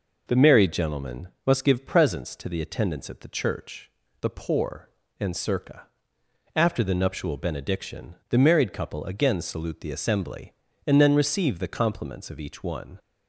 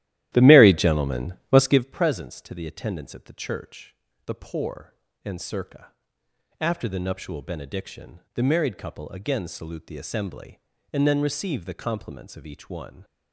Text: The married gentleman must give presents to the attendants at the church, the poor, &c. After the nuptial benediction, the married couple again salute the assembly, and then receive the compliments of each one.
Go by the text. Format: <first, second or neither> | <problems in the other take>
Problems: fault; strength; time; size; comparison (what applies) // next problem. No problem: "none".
first | starts louder than the rest; strong; until 1.9 s; 13.5 dB // pauses between "gentleman" and "must"; slight; at 1.3 s; 0.16 s long; slight in the first